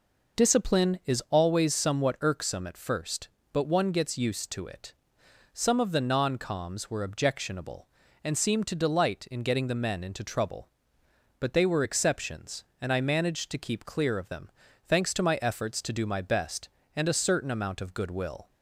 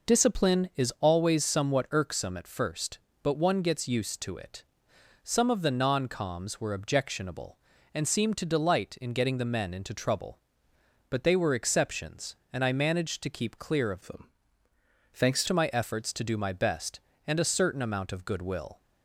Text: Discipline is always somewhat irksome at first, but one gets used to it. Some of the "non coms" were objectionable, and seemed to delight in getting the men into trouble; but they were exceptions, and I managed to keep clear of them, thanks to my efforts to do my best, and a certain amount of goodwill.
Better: first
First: none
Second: changes voice from "them" to "thanks"; from 14.0 to 15.4 s; 1.4 s long

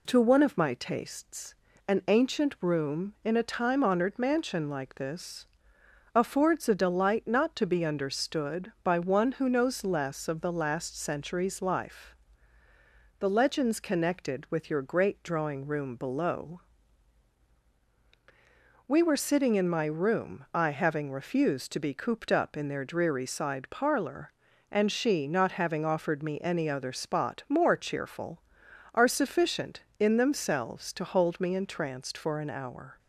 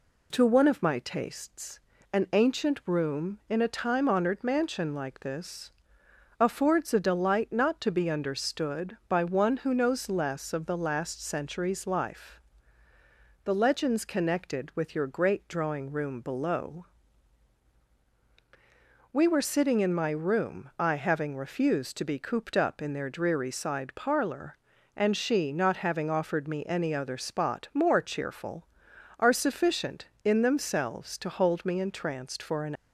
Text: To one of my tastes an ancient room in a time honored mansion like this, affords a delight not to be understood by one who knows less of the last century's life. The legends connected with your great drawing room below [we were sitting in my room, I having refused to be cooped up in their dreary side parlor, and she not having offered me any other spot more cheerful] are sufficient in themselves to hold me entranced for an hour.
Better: first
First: pauses between "tastes" and "an"; slight; at 1.5 s; 0.34 s long // pauses between "below" and "we"; strong; at 16.6 s; 2.2 s long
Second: pauses between "tastes" and "an"; slight; at 1.7 s; 0.34 s long // pauses between "below" and "we"; strong; at 16.8 s; 2.2 s long // stops before "hour"; at 32.7 s

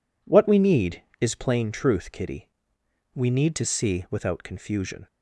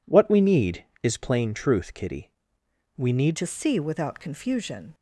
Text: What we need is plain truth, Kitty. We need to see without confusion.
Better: first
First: none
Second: changes voice at "to"; from 3.3 s on; 1.6 s long

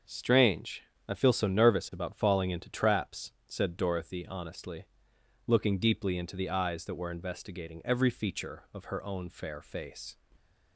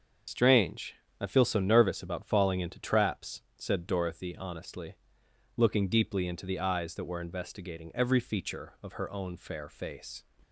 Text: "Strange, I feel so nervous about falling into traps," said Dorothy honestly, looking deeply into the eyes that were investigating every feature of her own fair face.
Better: first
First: starts louder than the rest; until 1.3 s; 6.5 dB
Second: loses the start of "Strange"; at 0.2 s; 80 ms // starts louder than the rest; until 1.5 s; 6.5 dB

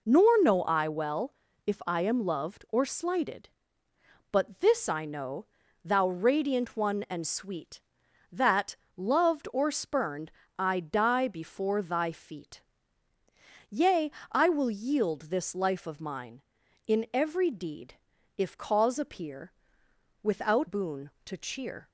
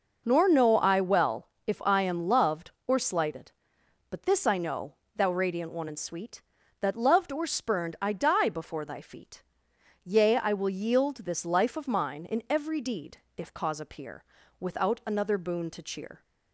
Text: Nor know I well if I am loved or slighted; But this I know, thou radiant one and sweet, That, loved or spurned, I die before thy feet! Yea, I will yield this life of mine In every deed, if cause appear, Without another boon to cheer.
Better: second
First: pauses between "well" and "if"; slight; at 1.3 s; 0.32 s long // skips "another"; at 20.6 s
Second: pauses between "well" and "if"; slight; at 1.4 s; 0.18 s long

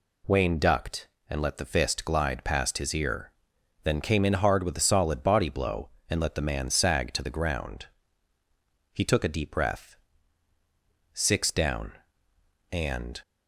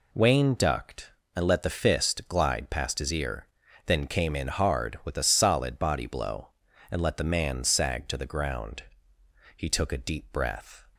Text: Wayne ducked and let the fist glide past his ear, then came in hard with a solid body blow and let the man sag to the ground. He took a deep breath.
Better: second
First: goes on to say "Six down and"; strong; from 11.1 s on; 2.0 s long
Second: none

